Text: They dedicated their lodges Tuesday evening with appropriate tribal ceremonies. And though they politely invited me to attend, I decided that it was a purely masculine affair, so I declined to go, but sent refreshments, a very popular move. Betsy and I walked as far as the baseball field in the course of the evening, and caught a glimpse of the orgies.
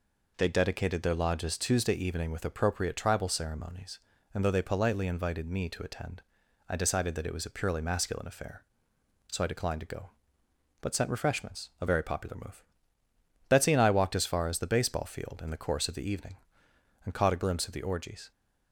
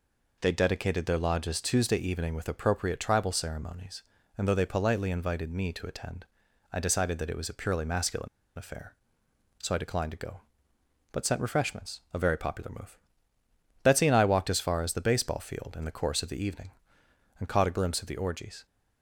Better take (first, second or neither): first